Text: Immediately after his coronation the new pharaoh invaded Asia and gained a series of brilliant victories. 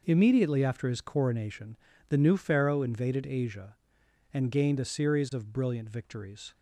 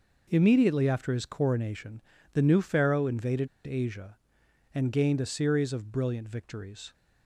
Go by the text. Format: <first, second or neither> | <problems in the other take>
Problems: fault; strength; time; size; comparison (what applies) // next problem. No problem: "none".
first | pauses between "coronation" and "the"; slight; at 2.0 s; 0.32 s long; slight in the first // pauses between "invaded" and "Asia"; slight; at 3.4 s; 0.18 s long